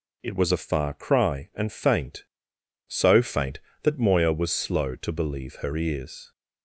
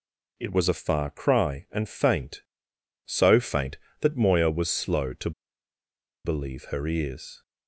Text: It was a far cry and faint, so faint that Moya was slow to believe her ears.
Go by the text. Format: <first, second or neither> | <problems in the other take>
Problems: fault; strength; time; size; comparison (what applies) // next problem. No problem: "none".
first | pauses between "to" and "believe"; noticeable; at 5.3 s; 0.94 s long